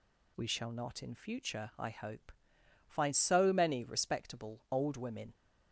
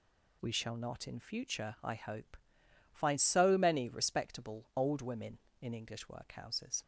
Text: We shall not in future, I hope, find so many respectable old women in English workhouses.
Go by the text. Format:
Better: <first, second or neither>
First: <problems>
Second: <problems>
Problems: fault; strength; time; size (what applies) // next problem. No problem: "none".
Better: second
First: stops before "in English workhouses"; at 5.3 s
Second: none